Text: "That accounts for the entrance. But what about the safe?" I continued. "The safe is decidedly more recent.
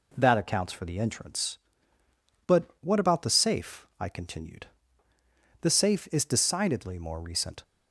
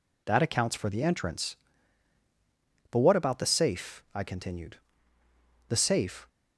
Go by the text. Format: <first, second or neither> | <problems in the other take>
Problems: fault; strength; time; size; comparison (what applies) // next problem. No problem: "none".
first | stops before "is decidedly more recent"; at 6.2 s